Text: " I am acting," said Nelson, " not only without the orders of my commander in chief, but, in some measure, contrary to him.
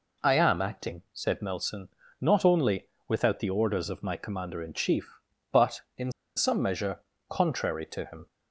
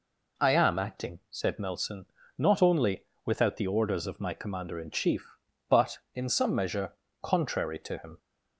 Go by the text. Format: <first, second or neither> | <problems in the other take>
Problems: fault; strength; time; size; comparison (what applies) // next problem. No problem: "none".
second | pauses between "only" and "without"; slight; at 2.8 s; 0.18 s long; slight in the second // pauses between "in" and "some"; slight; at 6.0 s; 0.26 s long